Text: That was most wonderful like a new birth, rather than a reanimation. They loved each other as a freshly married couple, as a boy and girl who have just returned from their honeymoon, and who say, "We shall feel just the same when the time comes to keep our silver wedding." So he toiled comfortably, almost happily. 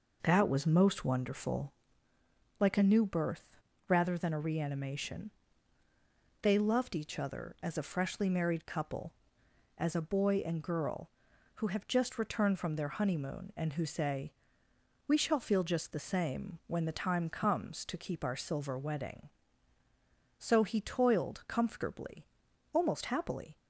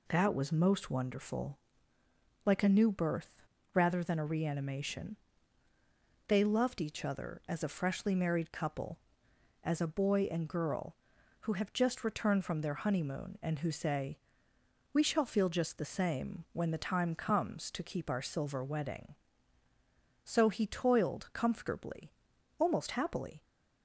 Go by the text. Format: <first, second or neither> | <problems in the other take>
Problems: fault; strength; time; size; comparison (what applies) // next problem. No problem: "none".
second | starts louder than the rest; noticeable; until 1.9 s; 5 dB // pauses between "wonderful" and "like"; noticeable; at 1.7 s; 0.86 s long; noticeable in the second